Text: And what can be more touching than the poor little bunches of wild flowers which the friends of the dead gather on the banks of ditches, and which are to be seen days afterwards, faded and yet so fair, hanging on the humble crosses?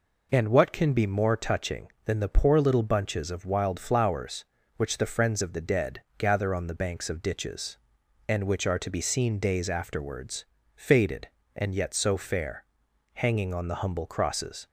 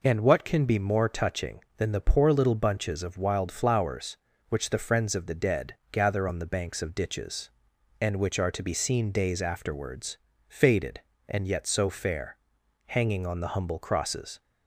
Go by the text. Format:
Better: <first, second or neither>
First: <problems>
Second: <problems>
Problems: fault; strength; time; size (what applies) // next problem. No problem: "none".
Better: neither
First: pauses between "dead" and "gather"; slight; at 6.0 s; 0.16 s long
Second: pauses between "dead" and "gather"; slight; at 5.7 s; 0.16 s long